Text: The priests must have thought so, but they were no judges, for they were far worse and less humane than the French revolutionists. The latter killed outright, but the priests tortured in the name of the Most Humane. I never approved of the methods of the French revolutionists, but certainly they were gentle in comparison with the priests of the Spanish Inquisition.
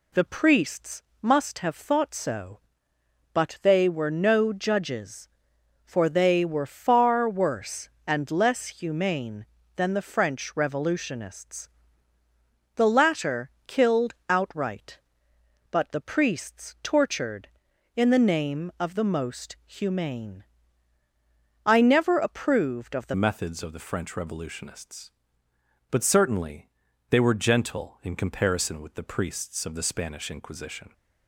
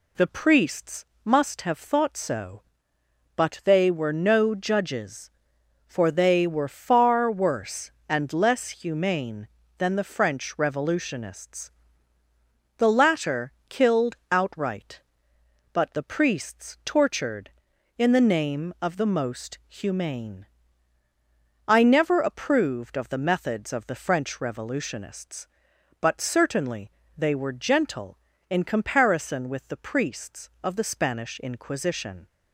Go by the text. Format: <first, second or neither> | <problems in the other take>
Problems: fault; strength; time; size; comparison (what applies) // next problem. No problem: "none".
second | pauses between "priests" and "must"; slight; at 1.0 s; 0.20 s long; slight in the second // pauses between "latter" and "killed"; slight; at 13.4 s; 0.18 s long; slight in the second // pauses between "killed" and "outright"; slight; at 14.1 s; 0.16 s long; slight in the second // changes voice at "methods"; from 23.1 s on; 7.8 s long // pauses between "certainly" and "they"; at 26.6 s; 0.40 s long; slight in the second